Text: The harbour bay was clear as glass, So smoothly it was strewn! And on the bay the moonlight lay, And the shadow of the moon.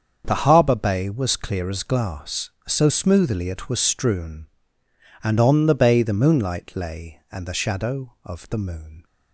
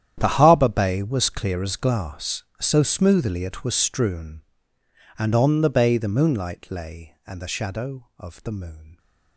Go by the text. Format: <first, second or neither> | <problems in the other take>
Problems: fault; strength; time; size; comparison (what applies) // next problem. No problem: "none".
first | gets quieter; strong; throughout; 17.5 dB // starts louder than the rest; strong; until 1.1 s; 10 dB; also in the first